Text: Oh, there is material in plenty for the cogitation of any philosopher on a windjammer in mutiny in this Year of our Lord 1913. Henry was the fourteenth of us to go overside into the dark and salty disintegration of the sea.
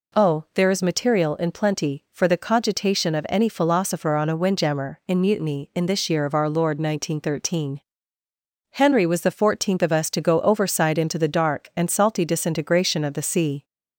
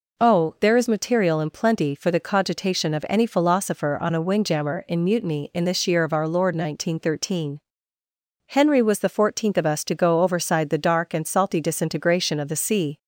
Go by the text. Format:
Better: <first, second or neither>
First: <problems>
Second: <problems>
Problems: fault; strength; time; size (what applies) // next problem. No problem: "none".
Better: first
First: none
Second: skips "into"; at 10.6 s